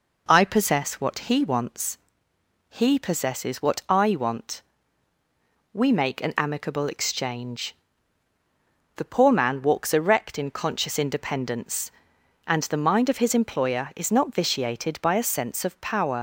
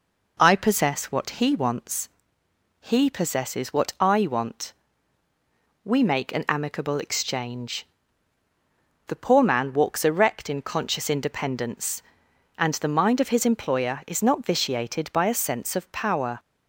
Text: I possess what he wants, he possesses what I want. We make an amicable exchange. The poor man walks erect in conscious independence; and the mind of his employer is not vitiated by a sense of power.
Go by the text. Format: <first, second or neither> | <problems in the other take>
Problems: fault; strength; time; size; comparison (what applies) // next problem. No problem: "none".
second | leaves "power" unfinished; at 16.1 s; 55 ms